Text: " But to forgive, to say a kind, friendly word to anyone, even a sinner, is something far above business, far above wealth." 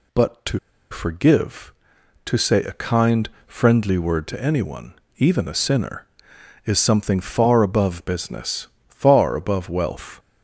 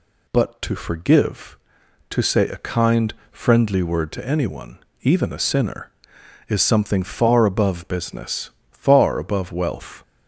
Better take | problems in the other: second | pauses between "to" and "forgive"; slight; at 0.5 s; 0.33 s long

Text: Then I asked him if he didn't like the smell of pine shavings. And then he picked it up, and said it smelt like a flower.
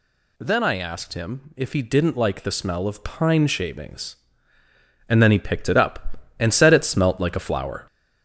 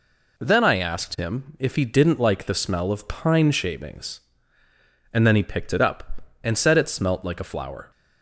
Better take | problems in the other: second | gets louder; noticeable; throughout; 4.5 dB

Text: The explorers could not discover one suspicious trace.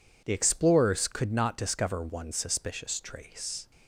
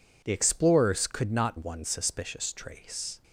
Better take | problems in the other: first | skips "discover"; at 1.5 s

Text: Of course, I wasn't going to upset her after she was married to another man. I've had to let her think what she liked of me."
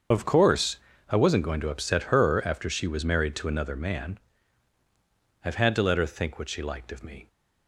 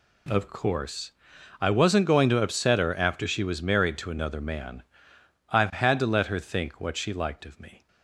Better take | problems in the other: second | loses the start of "Of"; at 0.1 s; 85 ms // starts louder than the rest; until 1.4 s; 6.5 dB

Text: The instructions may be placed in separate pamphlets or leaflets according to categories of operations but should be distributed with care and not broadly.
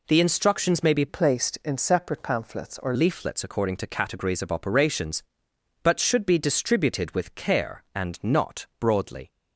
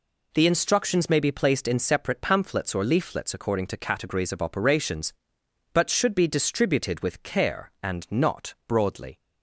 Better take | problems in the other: second | changes voice from "placed" to "or"; from 1.0 to 2.9 s; 1.9 s long

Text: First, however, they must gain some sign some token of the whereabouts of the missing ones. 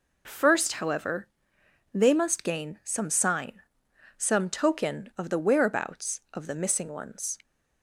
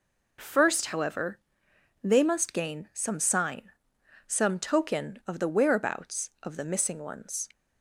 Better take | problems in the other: neither | pauses between "sign" and "some"; noticeable; the same in both

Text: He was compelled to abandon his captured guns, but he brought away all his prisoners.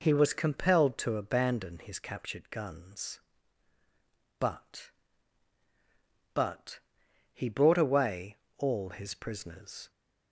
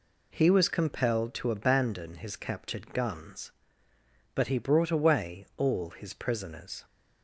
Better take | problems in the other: second | says "but" twice; at 6.3 s // pauses between "away" and "all"; slight; at 8.3 s; 0.22 s long

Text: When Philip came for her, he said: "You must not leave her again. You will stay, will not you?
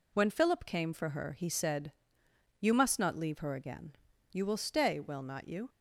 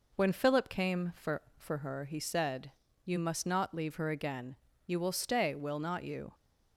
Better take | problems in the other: first | says "for" twice; at 1.5 s

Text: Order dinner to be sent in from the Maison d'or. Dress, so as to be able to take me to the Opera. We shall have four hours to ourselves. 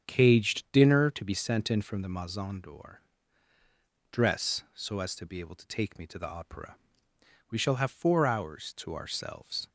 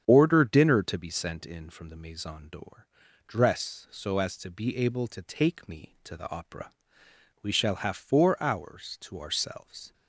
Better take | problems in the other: second | starts louder than the rest; strong; until 1.0 s; 7 dB; strong in the second // says "Caged" for "Order"; at 0.0 s

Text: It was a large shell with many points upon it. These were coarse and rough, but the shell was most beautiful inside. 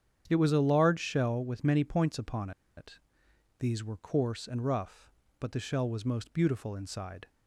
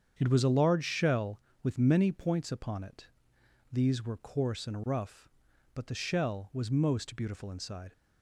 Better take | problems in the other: second | starts louder than the rest; strong; until 1.2 s; 9 dB; strong in the second // pauses between "upon" and "it"; slight; at 2.5 s; 0.26 s long

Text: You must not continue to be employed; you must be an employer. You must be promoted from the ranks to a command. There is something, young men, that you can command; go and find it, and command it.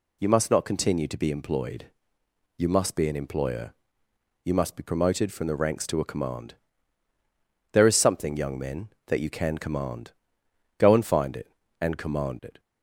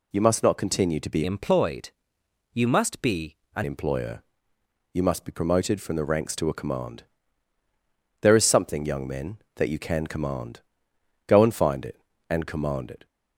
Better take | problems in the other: first | changes voice from "employed" to "an"; from 1.2 to 3.6 s; 2.4 s long // pauses between "be" and "an"; slight; at 3.3 s; 0.20 s long

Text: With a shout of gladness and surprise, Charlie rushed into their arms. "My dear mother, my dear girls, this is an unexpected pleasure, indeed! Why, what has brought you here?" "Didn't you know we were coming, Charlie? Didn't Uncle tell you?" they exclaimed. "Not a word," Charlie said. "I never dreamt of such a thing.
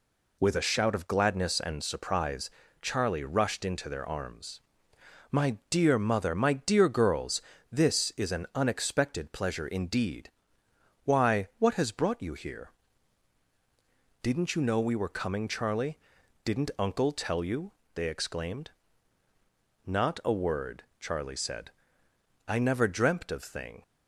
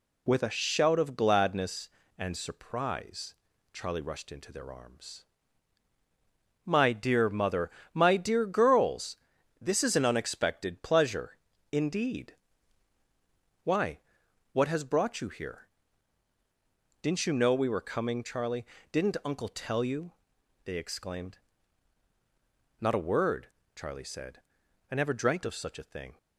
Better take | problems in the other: second | skips "such a"; at 23.4 s

